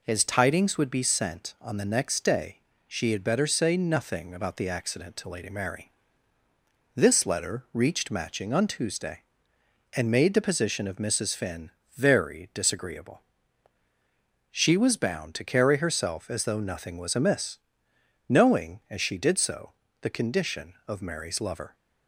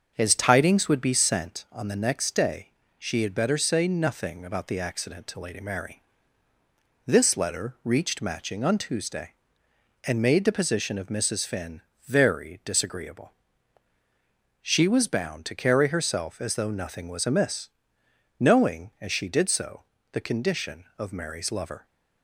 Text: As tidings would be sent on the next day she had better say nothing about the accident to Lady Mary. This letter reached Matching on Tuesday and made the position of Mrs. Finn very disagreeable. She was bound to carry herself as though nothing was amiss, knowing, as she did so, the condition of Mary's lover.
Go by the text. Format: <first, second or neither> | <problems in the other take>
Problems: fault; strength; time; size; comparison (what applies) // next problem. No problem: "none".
first | starts louder than the rest; until 1.5 s; 6.5 dB // pauses between "day" and "she"; slight; at 2.6 s; 0.30 s long; slight in the first // pauses between "Finn" and "very"; slight; at 11.8 s; 0.24 s long; slight in the first